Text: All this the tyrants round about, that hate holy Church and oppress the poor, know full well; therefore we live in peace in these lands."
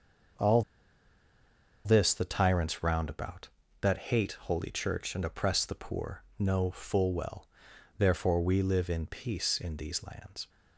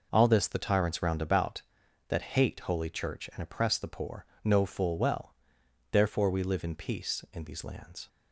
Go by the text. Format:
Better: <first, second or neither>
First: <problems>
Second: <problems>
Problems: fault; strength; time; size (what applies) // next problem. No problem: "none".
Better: second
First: starts louder than the rest; until 2.6 s; 6.5 dB // pauses between "All" and "this"; at 0.6 s; 1.2 s long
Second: none